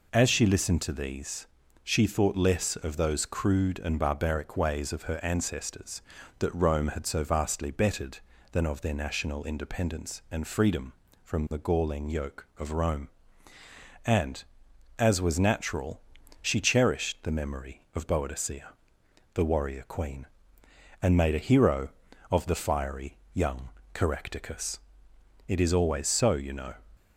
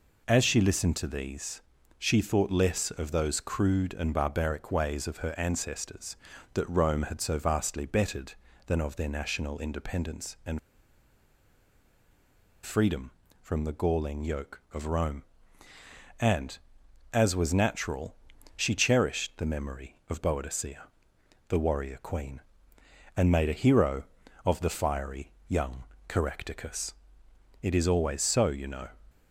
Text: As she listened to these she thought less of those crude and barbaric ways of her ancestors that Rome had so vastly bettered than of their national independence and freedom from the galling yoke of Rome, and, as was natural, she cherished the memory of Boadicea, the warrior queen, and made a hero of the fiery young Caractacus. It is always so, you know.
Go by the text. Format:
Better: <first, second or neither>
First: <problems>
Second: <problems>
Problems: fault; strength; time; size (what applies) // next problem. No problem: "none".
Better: first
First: pauses between "these" and "she"; at 1.4 s; 0.38 s long // pauses between "fiery" and "young"; slight; at 23.1 s; 0.18 s long // pauses between "young" and "Caractacus"; slight; at 23.6 s; 0.24 s long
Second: pauses between "these" and "she"; at 1.6 s; 0.38 s long // pauses between "and" and "freedom"; strong; at 10.5 s; 2.0 s long // pauses between "fiery" and "young"; slight; at 25.3 s; 0.18 s long // pauses between "young" and "Caractacus"; slight; at 25.8 s; 0.24 s long